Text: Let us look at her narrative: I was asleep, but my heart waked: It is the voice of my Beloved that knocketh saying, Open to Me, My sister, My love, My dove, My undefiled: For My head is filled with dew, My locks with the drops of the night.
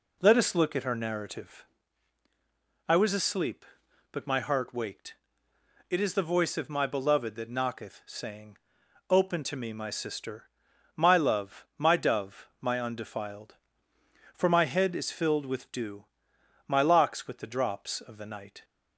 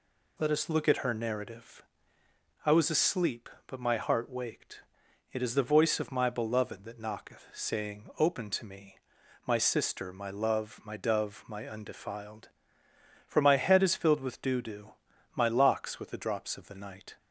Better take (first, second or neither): first